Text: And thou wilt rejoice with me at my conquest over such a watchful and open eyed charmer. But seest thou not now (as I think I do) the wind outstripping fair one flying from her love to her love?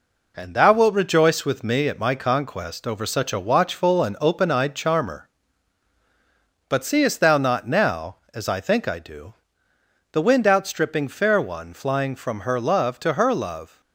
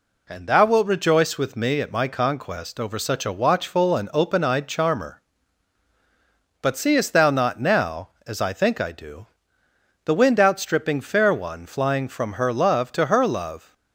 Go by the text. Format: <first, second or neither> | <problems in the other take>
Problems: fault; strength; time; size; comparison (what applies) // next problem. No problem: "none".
second | gets quieter; noticeable; throughout; 4.5 dB